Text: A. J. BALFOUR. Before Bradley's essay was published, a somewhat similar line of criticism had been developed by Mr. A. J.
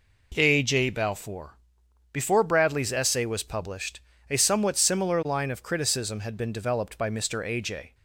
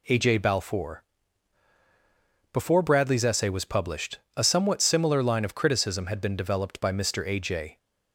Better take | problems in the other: neither | none

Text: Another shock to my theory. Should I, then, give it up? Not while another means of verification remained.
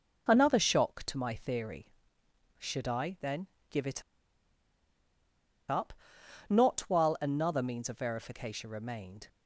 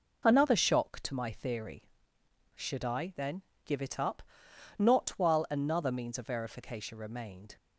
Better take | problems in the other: second | pauses between "it" and "up"; strong; at 4.0 s; 1.6 s long

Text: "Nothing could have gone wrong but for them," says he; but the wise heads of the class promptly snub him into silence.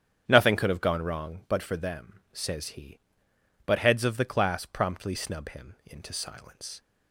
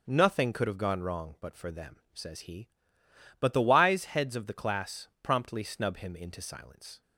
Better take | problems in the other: second | starts louder than the rest; strong; until 1.2 s; 9 dB; also in the second // skips "the wise"; at 3.7 s

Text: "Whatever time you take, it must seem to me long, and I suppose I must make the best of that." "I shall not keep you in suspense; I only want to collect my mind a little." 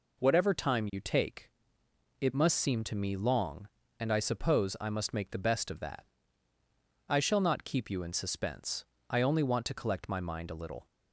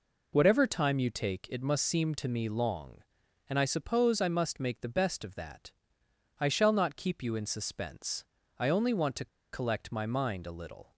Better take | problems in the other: first | pauses between "to" and "collect"; slight; at 9.2 s; 0.24 s long

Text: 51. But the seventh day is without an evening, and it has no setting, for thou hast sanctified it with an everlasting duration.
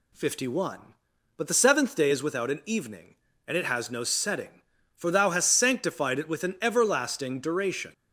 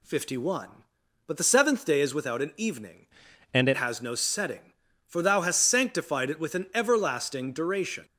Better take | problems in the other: first | changes voice from "and" to "it"; from 3.5 to 3.7 s; 0.2 s long

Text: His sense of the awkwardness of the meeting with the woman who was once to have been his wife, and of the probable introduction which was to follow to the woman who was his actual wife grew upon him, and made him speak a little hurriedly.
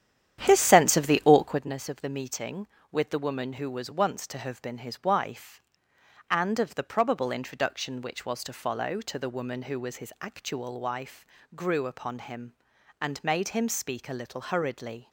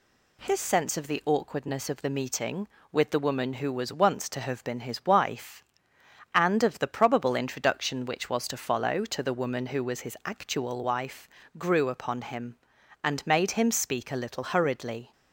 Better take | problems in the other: second | starts louder than the rest; strong; until 1.8 s; 10 dB // pauses between "wife" and "grew"; slight; at 11.2 s; 0.28 s long; slight in the second

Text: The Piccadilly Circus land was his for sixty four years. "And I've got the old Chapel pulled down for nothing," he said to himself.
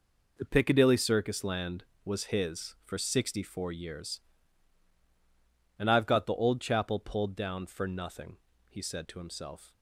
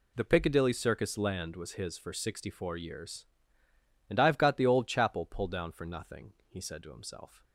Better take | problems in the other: neither | none

